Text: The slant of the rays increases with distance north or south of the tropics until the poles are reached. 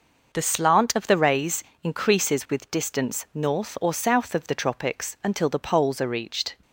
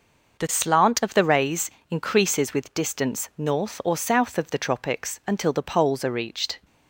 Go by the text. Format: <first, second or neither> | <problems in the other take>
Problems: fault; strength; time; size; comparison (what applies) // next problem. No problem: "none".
neither | pauses between "rays" and "increases"; slight; the same in both